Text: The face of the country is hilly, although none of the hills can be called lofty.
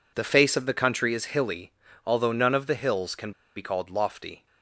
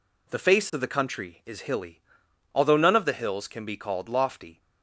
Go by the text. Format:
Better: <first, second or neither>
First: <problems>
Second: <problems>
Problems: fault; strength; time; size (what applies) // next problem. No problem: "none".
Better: second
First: pauses between "can" and "be"; slight; at 3.3 s; 0.25 s long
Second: none